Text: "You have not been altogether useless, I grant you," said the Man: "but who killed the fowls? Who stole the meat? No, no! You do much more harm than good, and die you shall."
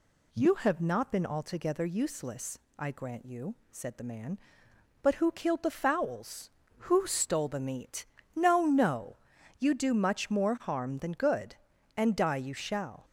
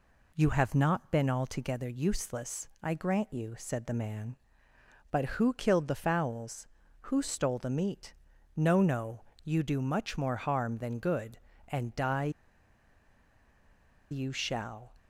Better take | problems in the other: first | pauses between "die" and "you"; strong; at 12.3 s; 1.8 s long

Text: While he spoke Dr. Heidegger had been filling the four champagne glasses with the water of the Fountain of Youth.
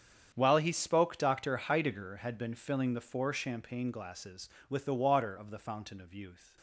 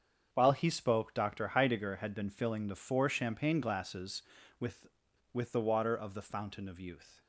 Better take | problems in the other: first | starts louder than the rest; strong; until 1.3 s; 7 dB; strong in the first // says "with" twice; at 5.3 s

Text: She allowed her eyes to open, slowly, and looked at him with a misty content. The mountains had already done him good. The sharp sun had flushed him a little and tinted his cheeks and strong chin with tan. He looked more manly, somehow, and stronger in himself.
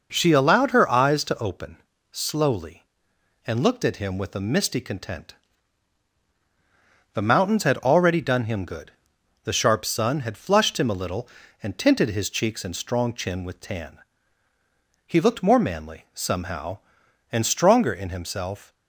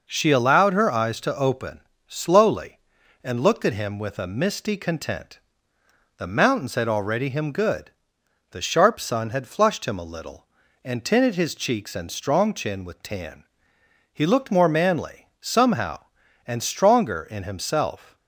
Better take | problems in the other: first | skips "done"; at 7.2 s

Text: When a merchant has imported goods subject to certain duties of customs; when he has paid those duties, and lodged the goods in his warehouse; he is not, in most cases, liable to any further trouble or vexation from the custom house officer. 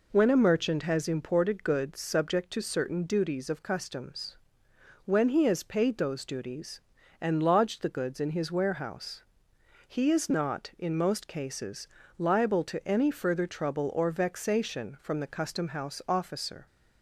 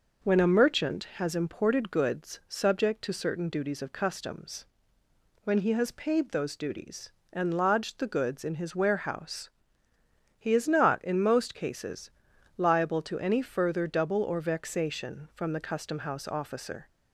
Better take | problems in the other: first | says "double" for "trouble"; at 13.8 s

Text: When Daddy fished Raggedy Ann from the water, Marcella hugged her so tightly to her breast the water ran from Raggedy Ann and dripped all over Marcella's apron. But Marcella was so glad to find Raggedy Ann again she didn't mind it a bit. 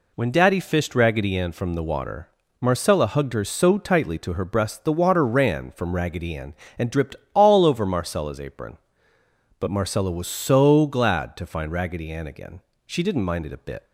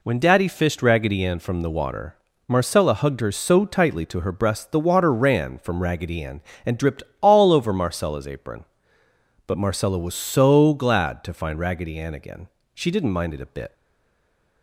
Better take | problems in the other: first | pauses between "dripped" and "all"; slight; at 7.0 s; 0.18 s long; slight in the first // pauses between "again" and "she"; slight; at 12.4 s; 0.26 s long; slight in the first // stays silent after the last word; slight; from 13.7 s on; 0.9 s long

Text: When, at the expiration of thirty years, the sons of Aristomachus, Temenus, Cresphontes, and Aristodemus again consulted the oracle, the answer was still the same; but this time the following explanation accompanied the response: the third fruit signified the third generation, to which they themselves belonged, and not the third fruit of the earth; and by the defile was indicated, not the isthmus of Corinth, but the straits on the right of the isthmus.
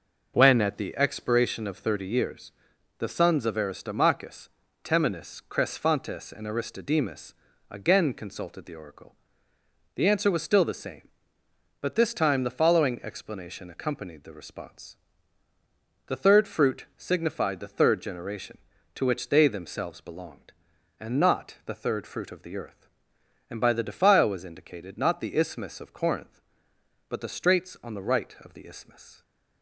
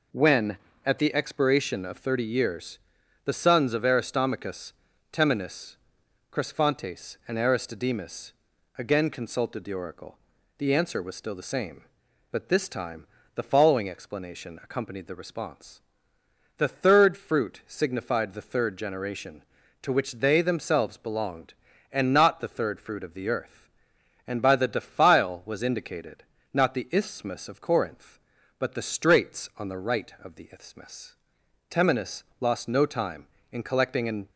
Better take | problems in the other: first | pauses between "Aristodemus" and "again"; at 8.3 s; 0.44 s long; slight in the first // pauses between "time" and "the"; slight; at 13.0 s; 0.30 s long // goes on to say "Temenus lost no time in collecting an"; strong; from 31.6 s on; 2.6 s long

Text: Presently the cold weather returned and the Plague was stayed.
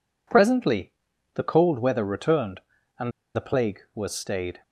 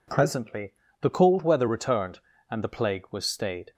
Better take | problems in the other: second | pauses between "Presently" and "the"; at 0.9 s; 0.44 s long; slight in the second // pauses between "and" and "the"; slight; at 3.1 s; 0.24 s long

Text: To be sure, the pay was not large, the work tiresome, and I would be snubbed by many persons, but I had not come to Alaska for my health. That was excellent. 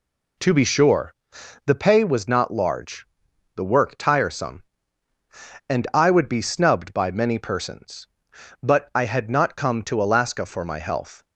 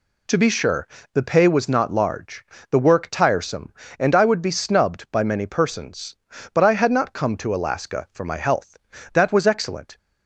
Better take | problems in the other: second | stops before "That was excellent"; at 11.2 s

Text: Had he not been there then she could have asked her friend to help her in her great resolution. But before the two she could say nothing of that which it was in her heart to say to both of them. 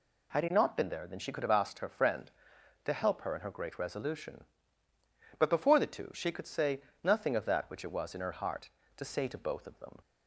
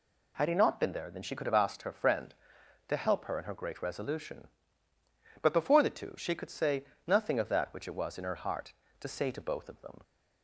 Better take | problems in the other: neither | pauses between "say" and "nothing"; slight; the same in both

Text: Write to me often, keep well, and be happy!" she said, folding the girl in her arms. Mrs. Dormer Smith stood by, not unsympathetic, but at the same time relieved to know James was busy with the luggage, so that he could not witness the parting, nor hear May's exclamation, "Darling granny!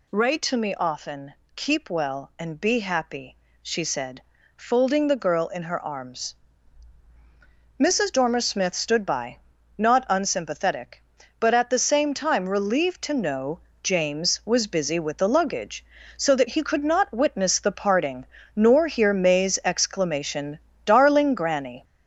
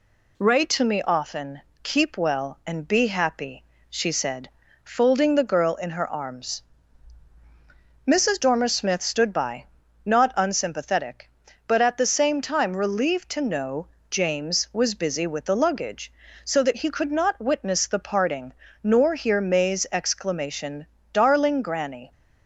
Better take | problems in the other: second | gets louder; noticeable; throughout; 5.5 dB // pauses between "know" and "James"; slight; at 13.5 s; 0.22 s long; slight in the second

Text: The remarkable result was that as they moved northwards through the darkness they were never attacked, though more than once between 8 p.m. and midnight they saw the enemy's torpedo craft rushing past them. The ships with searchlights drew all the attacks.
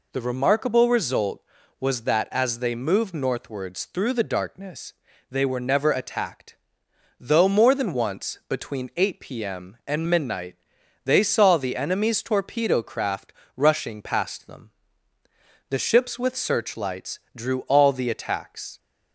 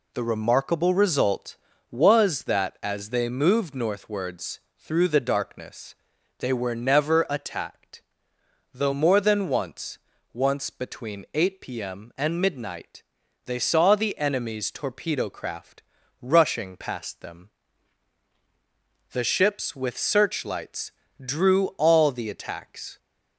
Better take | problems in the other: first | pauses between "northwards" and "through"; slight; at 4.5 s; 0.18 s long // pauses between "darkness" and "they"; noticeable; at 5.9 s; 0.46 s long; slight in the first // says "once" twice; at 10.3 s // pauses between "midnight" and "they"; at 13.0 s; 0.42 s long; noticeable in the first // pauses between "craft" and "rushing"; at 15.8 s; 0.40 s long; slight in the first // pauses between "searchlights" and "drew"; slight; at 20.9 s; 0.32 s long; slight in the first

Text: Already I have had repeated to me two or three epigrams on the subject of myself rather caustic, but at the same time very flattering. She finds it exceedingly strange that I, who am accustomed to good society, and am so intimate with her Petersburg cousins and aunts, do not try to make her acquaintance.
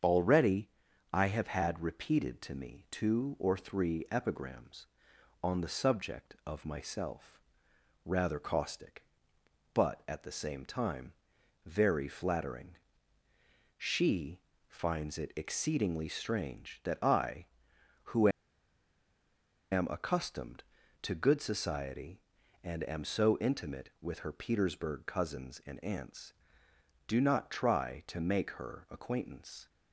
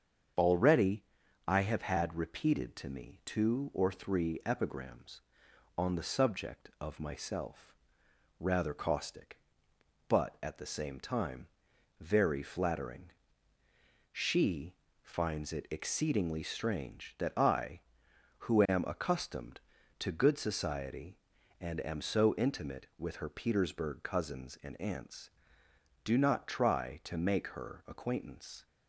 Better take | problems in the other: second | starts louder than the rest; strong; until 1.4 s; 7.5 dB; strong in the second // pauses between "Already" and "I"; at 0.7 s; 0.42 s long; also in the second // pauses between "myself" and "rather"; noticeable; at 7.4 s; 0.64 s long; noticeable in the second // pauses between "time" and "very"; noticeable; at 11.1 s; 0.54 s long; noticeable in the second // pauses between "She" and "finds"; slight; at 14.4 s; 0.28 s long; slight in the second // pauses between "who" and "am"; strong; at 18.2 s; 1.4 s long

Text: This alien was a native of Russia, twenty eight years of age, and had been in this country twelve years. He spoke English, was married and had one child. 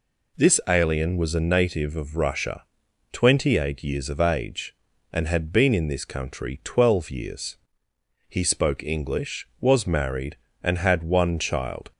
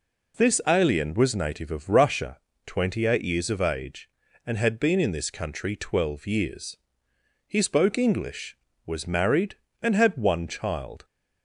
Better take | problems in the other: first | skips "a"; at 1.3 s

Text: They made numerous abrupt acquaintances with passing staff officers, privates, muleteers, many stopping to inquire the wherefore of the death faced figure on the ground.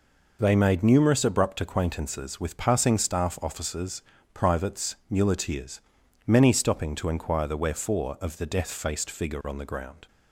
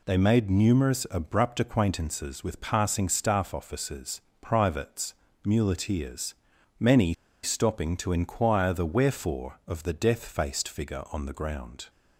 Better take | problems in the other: first | pauses between "many" and "stopping"; slight; at 7.1 s; 0.30 s long

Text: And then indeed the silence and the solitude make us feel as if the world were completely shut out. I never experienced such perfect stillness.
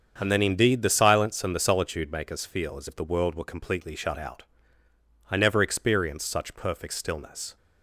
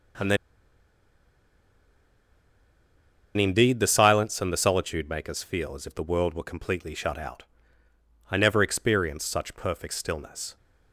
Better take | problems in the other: first | starts louder than the rest; strong; until 4.1 s; 7.5 dB; strong in the first // pauses between "then" and "indeed"; strong; at 0.3 s; 3.0 s long

